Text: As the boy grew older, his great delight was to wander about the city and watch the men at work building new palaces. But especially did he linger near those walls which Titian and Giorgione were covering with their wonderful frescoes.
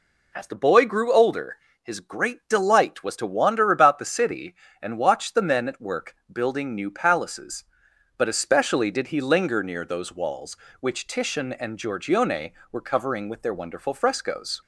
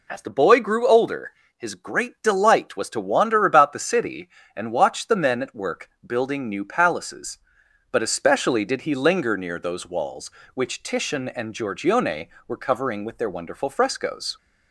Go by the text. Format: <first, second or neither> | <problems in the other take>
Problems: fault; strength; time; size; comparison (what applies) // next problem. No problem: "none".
neither | pauses between "work" and "building"; slight; the same in both